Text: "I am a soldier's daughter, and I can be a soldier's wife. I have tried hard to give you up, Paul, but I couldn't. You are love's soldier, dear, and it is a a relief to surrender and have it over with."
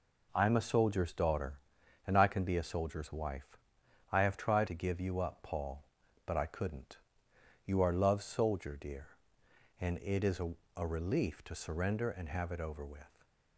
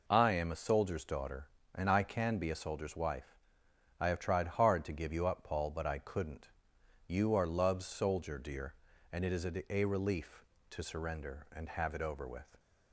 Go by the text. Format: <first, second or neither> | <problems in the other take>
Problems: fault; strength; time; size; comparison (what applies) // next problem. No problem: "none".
second | skips "hard"; at 4.6 s // pauses between "a" and "a"; slight; at 10.5 s; 0.24 s long